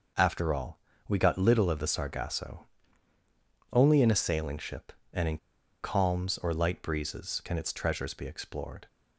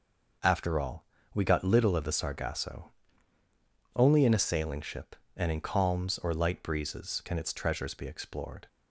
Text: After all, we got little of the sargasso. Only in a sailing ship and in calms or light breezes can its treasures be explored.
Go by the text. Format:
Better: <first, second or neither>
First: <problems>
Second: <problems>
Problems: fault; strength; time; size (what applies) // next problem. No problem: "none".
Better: second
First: pauses between "in" and "calms"; at 5.3 s; 0.44 s long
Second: none